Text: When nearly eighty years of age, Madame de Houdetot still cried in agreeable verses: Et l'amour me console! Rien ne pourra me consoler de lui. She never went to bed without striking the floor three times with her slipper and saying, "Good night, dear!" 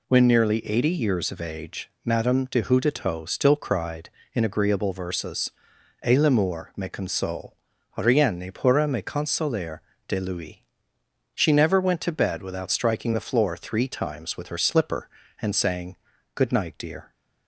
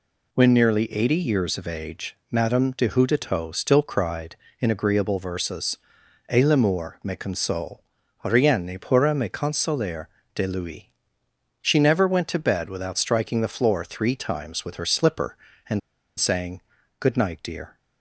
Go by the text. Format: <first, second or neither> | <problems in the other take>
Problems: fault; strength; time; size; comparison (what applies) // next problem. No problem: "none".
first | pauses between "consoler" and "de"; slight; at 10.0 s; 0.28 s long; slight in the first // pauses between "and" and "saying"; at 15.8 s; 0.39 s long